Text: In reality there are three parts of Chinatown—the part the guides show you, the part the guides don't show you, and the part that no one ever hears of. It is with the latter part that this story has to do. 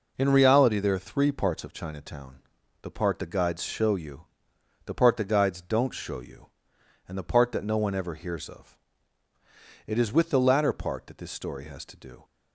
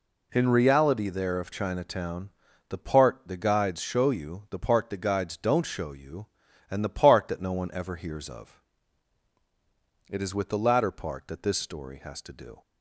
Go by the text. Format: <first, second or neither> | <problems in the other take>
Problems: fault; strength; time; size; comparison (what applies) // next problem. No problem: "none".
first | skips "are three parts"; at 1.4 s